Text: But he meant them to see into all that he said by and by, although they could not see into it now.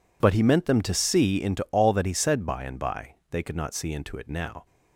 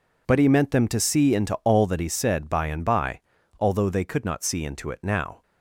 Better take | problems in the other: second | skips "although"; at 3.2 s

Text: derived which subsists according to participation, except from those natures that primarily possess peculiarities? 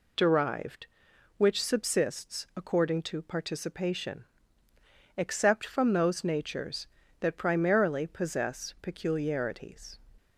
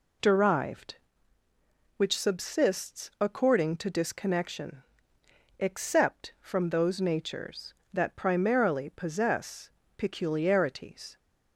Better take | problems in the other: first | says "disconnection" for "participation"; at 3.8 s // pauses between "possess" and "peculiarities"; slight; at 9.6 s; 0.26 s long

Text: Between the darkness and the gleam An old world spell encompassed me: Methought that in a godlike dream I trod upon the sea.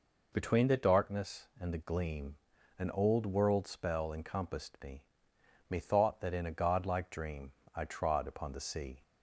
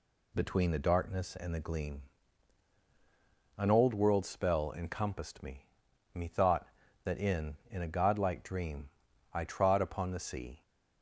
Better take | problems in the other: first | pauses between "gleam" and "An"; strong; at 2.0 s; 1.5 s long; also in the first // says "in" twice; at 7.6 s // pauses between "dream" and "I"; noticeable; at 8.8 s; 0.46 s long; slight in the first

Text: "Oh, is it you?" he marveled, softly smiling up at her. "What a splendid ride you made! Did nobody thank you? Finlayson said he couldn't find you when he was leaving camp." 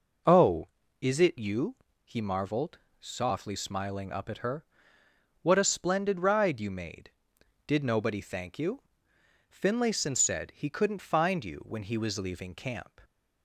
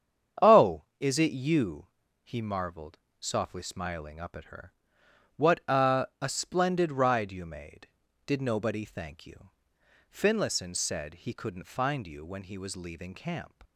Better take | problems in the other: first | starts louder than the rest; strong; until 1.5 s; 8 dB // says "a" twice; at 6.2 s

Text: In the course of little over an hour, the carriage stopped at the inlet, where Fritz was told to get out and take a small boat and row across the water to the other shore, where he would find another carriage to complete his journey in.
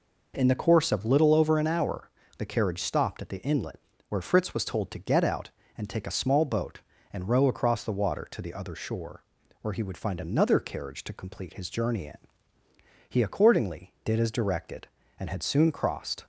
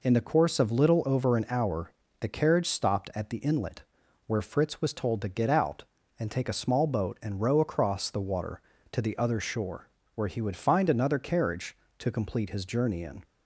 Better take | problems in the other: second | goes on to say "He accordingly did as directed and had soon crossed"; strong; from 13.0 s on; 3.1 s long

